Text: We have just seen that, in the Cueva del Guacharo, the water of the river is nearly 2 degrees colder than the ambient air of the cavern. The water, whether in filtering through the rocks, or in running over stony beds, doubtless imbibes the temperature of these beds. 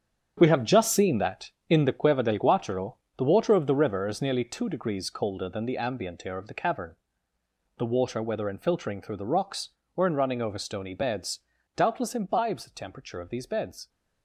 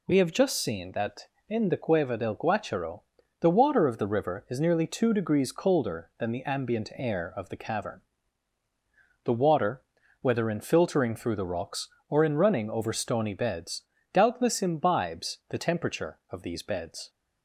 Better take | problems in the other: second | gets quieter; strong; throughout; 11 dB

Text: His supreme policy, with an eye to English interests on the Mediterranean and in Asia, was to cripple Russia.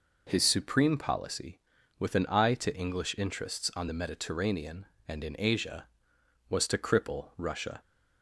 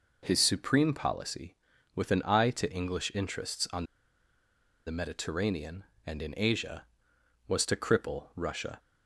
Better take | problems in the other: first | pauses between "on" and "the"; at 3.8 s; 1.0 s long

